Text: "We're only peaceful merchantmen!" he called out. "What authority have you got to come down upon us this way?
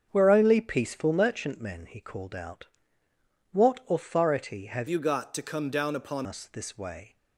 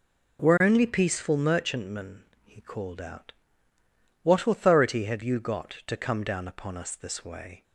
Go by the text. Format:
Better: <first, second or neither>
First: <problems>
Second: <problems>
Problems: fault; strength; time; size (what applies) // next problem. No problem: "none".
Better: second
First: starts louder than the rest; strong; until 1.1 s; 7.5 dB // changes voice from "you" to "upon"; from 4.8 to 6.2 s; 1.4 s long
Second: none